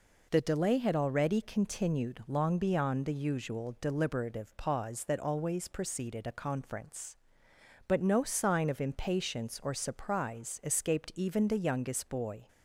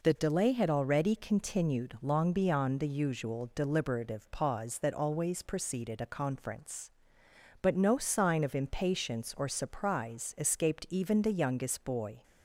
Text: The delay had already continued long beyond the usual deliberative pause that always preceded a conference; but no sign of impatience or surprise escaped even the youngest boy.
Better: neither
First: none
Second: none

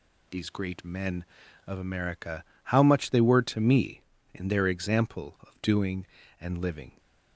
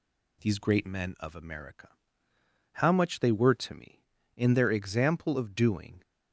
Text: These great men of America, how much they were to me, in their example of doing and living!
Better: first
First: none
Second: stops before "and living"; at 6.0 s

